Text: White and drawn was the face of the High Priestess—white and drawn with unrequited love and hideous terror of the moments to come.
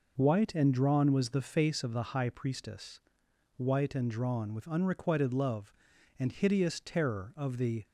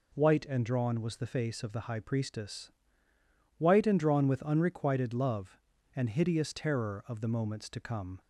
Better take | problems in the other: second | stops before "moments to come"; at 7.8 s

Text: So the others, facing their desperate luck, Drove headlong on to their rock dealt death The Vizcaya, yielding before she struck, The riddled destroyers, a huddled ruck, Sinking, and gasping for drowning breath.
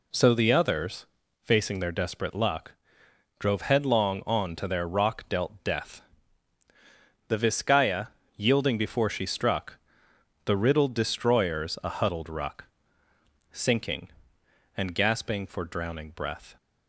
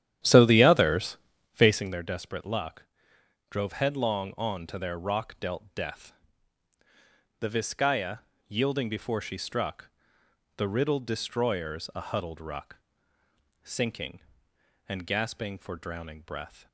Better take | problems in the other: first | starts louder than the rest; strong; until 2.0 s; 11 dB // pauses between "death" and "The"; strong; at 6.1 s; 1.2 s long; strong in the first

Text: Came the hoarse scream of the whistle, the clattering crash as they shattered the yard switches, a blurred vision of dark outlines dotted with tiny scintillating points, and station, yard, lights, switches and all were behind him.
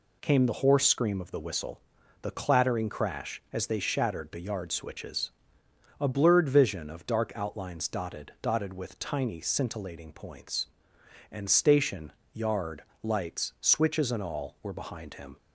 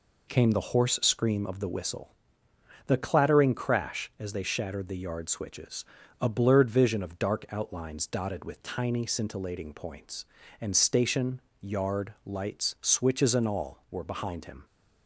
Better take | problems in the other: second | says "dotted" twice; at 8.4 s

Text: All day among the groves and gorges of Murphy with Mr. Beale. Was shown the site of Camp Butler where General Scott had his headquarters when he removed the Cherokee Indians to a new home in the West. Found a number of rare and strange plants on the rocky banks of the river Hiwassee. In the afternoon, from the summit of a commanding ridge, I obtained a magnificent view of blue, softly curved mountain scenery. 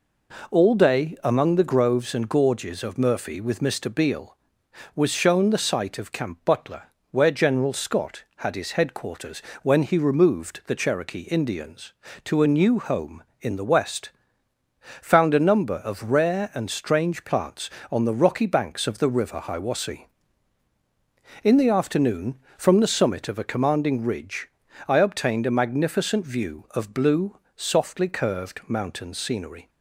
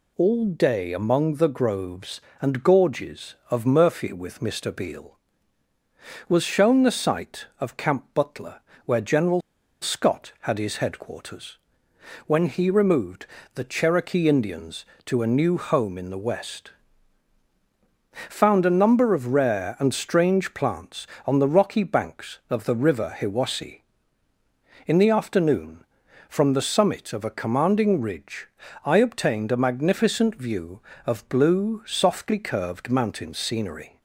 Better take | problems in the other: first | pauses between "Butler" and "where"; slight; at 8.5 s; 0.26 s long; slight in the first // pauses between "General" and "Scott"; at 9.4 s; 0.41 s long // pauses between "headquarters" and "when"; noticeable; at 11.5 s; 0.68 s long; slight in the first // pauses between "removed" and "the"; slight; at 13.2 s; 0.28 s long

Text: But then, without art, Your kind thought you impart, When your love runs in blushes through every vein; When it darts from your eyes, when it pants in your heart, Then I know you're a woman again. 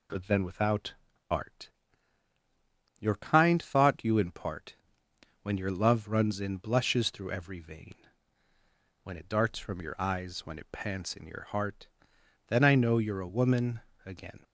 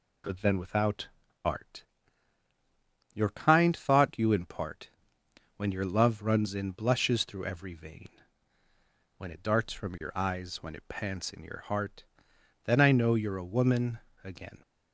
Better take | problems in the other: neither | pauses between "without" and "art"; the same in both // pauses between "woman" and "again"; slight; the same in both

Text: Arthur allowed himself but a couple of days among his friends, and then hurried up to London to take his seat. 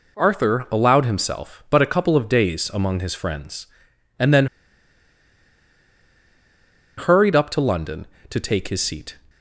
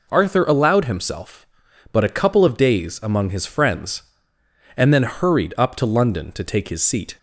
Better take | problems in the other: second | pauses between "then" and "hurried"; strong; at 4.4 s; 2.5 s long

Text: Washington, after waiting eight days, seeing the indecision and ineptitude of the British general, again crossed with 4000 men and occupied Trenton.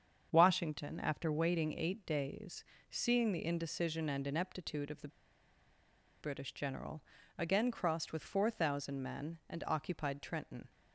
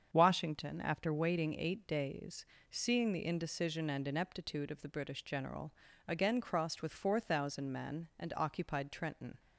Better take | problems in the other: second | starts louder than the rest; strong; until 1.3 s; 7 dB; strong in the second // pauses between "the" and "British"; at 5.0 s; 1.1 s long

